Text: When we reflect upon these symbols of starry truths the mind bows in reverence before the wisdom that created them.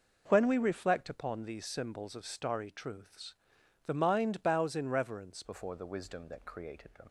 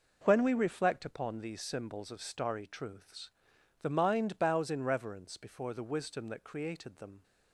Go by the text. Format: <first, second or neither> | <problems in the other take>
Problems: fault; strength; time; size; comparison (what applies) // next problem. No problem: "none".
second | pauses between "truths" and "the"; noticeable; at 3.3 s; 0.52 s long; noticeable in the second // changes voice at "before"; from 5.4 s on; 1.6 s long